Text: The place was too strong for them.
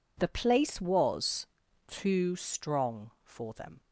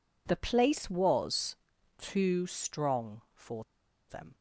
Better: first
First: pauses between "was" and "too"; at 1.4 s; 0.42 s long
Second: pauses between "was" and "too"; at 1.5 s; 0.44 s long // pauses between "for" and "them"; at 3.6 s; 0.45 s long

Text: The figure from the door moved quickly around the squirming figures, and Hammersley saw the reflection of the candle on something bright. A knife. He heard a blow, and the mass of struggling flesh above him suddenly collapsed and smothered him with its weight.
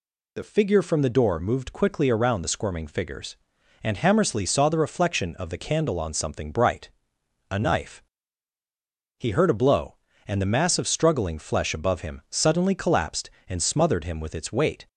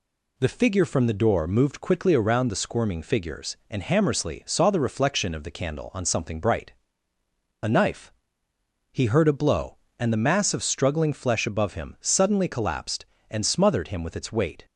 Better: neither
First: none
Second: none

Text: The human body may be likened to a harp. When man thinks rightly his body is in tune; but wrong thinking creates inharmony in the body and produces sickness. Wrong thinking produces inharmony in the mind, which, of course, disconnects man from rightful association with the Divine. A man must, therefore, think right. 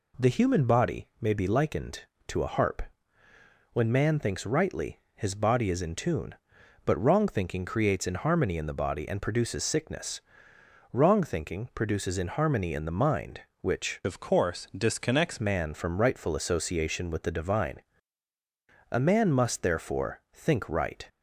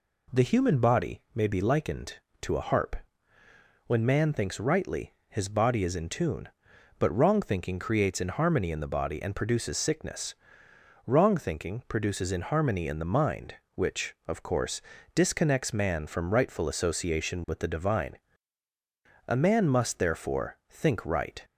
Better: second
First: pauses between "rightly" and "his"; slight; at 4.9 s; 0.16 s long // changes voice from "of" to "disconnects"; from 14.0 to 15.3 s; 1.3 s long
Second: pauses between "rightly" and "his"; slight; at 5.1 s; 0.16 s long

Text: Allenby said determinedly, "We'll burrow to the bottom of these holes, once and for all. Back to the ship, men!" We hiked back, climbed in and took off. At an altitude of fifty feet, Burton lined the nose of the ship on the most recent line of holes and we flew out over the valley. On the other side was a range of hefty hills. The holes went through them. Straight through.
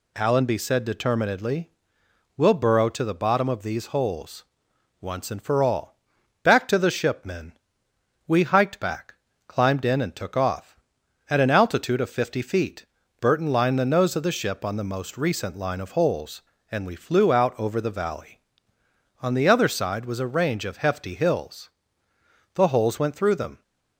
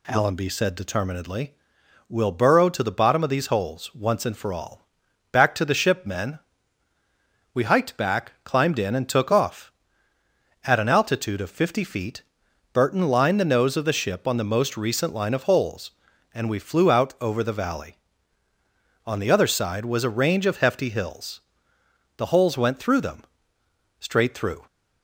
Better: second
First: stops before "Straight through"; at 23.6 s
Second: none

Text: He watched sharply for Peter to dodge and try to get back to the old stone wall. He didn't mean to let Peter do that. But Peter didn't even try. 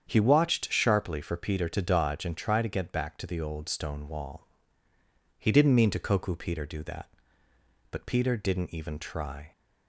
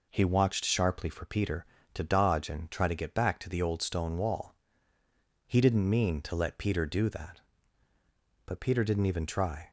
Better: second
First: starts louder than the rest; strong; until 1.1 s; 8 dB // says "koku" for "let"; at 5.9 s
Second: none

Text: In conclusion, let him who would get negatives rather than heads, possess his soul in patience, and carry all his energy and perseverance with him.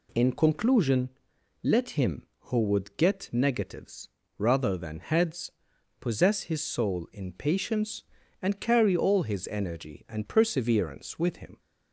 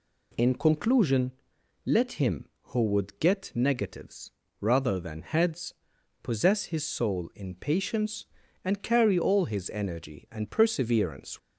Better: first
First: pauses between "negatives" and "rather"; slight; at 4.0 s; 0.30 s long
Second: pauses between "negatives" and "rather"; slight; at 4.3 s; 0.30 s long // stops before "with him"; at 11.3 s

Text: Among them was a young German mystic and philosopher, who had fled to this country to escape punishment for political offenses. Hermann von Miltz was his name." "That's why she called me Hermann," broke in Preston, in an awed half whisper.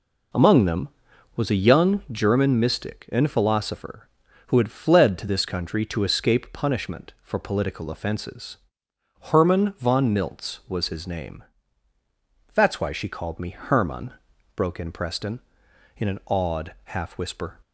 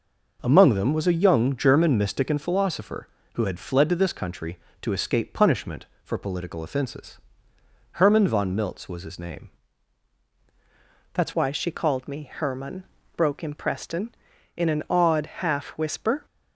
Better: first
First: none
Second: changes voice at "why"; from 11.3 s on; 4.9 s long

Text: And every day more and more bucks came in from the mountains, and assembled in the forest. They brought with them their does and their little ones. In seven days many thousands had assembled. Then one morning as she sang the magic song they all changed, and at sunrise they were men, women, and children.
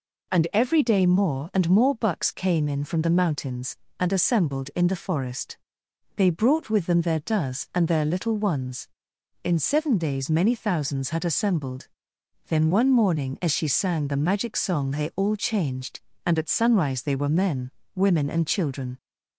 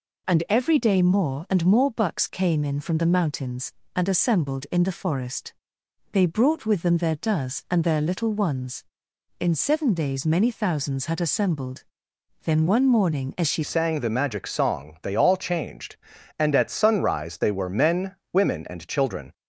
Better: first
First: none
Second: changes voice at "sang"; from 13.6 s on; 5.7 s long

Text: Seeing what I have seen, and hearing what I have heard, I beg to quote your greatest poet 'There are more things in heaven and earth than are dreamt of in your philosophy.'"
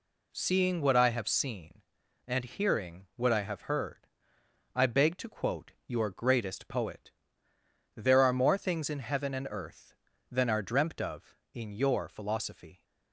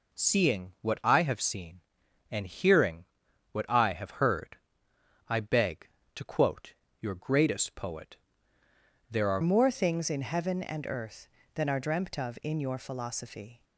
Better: first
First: pauses between "quote" and "your"; slight; at 5.7 s; 0.16 s long // pauses between "poet" and "There"; noticeable; at 7.1 s; 0.84 s long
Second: pauses between "hearing" and "what"; noticeable; at 3.0 s; 0.46 s long // pauses between "quote" and "your"; slight; at 6.7 s; 0.26 s long // pauses between "poet" and "There"; noticeable; at 8.1 s; 0.92 s long // changes voice at "more"; from 9.4 s on; 4.2 s long

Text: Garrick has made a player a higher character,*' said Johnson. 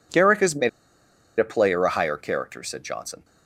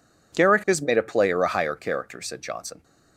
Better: second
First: pauses between "made" and "a"; noticeable; at 0.6 s; 0.70 s long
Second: none

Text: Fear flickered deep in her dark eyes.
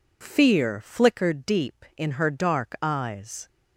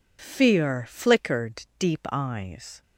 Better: first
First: none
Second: skips "in her dark"; at 2.0 s

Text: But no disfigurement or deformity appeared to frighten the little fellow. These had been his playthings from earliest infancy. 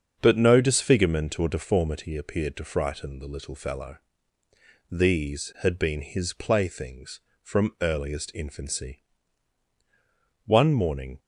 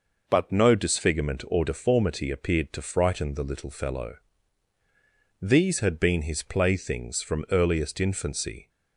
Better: second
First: starts louder than the rest; until 1.2 s; 7 dB // goes on to say "One morning"; noticeable; from 10.4 s on; 0.74 s long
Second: none

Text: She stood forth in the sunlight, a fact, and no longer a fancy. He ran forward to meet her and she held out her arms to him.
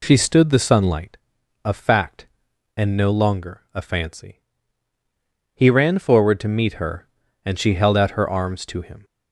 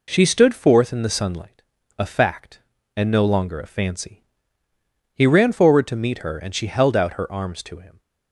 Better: second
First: skips "forth in"; at 0.4 s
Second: none

